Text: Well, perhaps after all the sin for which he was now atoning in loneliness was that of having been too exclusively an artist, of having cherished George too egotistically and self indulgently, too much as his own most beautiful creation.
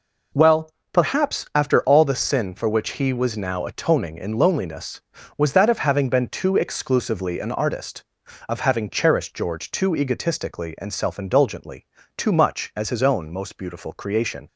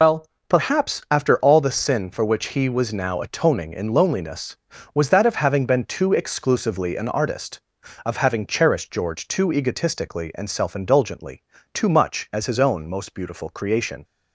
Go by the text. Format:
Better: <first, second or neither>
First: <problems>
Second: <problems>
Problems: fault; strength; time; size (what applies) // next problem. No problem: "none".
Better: first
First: none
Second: loses the start of "Well"; at 0.0 s; 105 ms